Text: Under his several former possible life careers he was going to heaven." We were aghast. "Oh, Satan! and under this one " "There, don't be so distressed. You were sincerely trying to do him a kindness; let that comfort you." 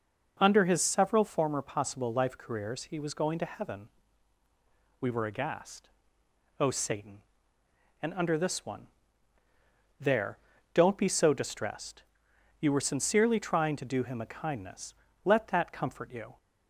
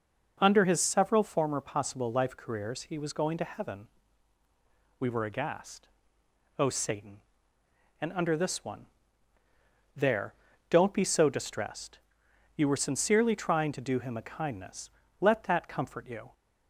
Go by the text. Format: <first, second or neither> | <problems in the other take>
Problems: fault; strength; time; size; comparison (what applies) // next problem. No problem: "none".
neither | starts louder than the rest; the same in both